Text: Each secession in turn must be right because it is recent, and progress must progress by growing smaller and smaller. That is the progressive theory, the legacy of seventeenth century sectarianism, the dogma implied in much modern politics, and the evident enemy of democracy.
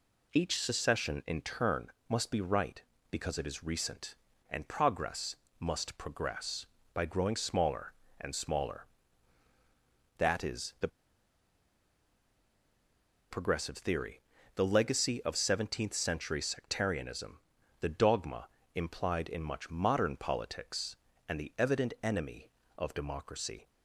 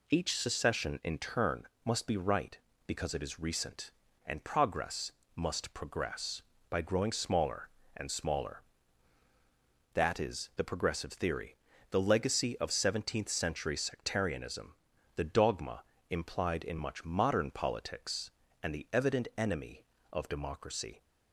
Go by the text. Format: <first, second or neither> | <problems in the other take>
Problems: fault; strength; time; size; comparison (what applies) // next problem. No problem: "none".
second | pauses between "turn" and "must"; slight; at 1.9 s; 0.16 s long; slight in the second // pauses between "progress" and "must"; slight; at 5.3 s; 0.24 s long; slight in the second // pauses between "the" and "progressive"; strong; at 10.8 s; 2.4 s long // pauses between "dogma" and "implied"; slight; at 18.4 s; 0.28 s long; slight in the second